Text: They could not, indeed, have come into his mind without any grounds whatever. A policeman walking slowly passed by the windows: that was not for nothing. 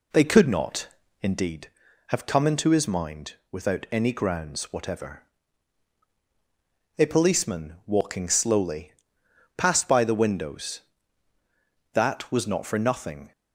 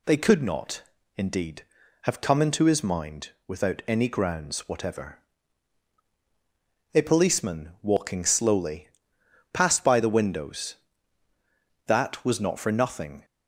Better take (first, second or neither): second